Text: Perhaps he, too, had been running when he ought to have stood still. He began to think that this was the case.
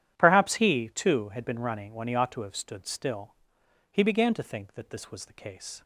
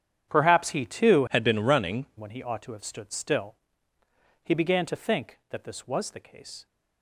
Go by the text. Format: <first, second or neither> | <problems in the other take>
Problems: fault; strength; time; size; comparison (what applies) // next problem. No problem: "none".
first | starts louder than the rest; strong; until 1.3 s; 9 dB; strong in the first // changes voice from "had" to "running"; from 1.2 to 2.0 s; 0.8 s long